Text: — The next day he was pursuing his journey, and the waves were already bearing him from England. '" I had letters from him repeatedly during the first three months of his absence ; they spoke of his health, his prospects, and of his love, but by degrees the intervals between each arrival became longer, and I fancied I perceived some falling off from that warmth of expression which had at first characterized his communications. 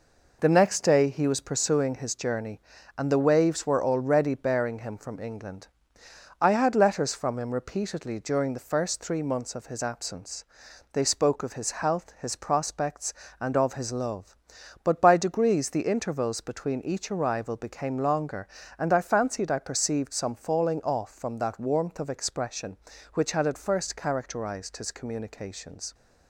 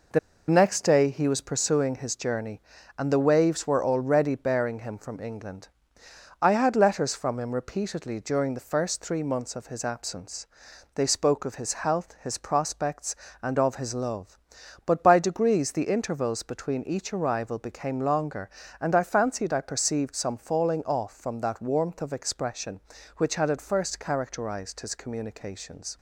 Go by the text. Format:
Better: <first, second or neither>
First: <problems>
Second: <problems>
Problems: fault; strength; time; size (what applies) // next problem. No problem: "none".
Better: first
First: pauses between "his" and "health"; slight; at 11.6 s; 0.16 s long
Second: pauses between "The" and "next"; slight; at 0.1 s; 0.29 s long // pauses between "his" and "health"; slight; at 11.7 s; 0.16 s long